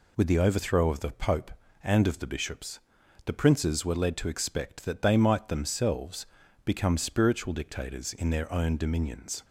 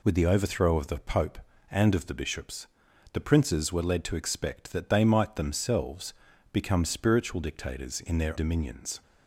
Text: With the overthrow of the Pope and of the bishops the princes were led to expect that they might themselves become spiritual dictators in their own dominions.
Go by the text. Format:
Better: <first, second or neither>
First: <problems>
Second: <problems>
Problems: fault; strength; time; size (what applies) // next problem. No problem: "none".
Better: first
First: pauses between "bishops" and "the"; noticeable; at 2.7 s; 0.46 s long // pauses between "themselves" and "become"; at 6.2 s; 0.38 s long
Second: pauses between "bishops" and "the"; noticeable; at 2.6 s; 0.46 s long // pauses between "themselves" and "become"; at 6.1 s; 0.38 s long // skips "own"; at 8.3 s